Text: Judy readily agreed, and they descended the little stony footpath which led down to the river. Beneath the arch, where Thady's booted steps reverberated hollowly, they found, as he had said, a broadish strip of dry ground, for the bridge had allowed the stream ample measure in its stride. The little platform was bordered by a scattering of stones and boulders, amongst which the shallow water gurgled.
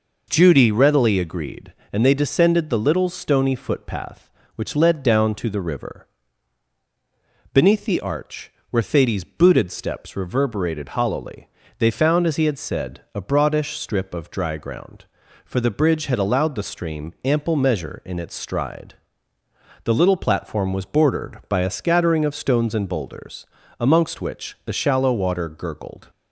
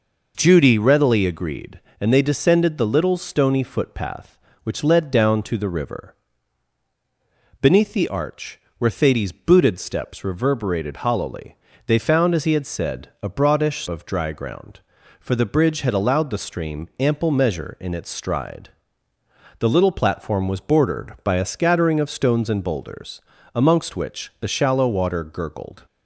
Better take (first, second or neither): first